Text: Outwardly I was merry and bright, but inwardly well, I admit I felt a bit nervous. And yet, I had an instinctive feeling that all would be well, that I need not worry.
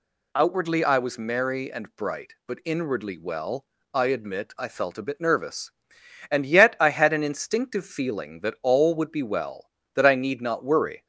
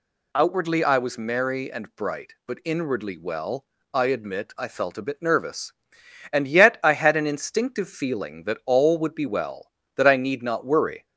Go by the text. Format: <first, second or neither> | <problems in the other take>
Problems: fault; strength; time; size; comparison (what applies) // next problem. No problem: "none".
neither | none